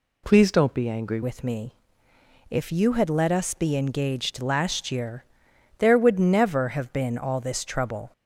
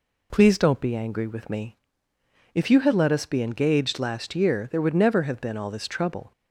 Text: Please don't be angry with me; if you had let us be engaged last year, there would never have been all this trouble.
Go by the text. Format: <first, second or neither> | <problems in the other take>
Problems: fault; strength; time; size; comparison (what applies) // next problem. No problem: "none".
second | changes voice at "with"; from 1.2 s on; 6.9 s long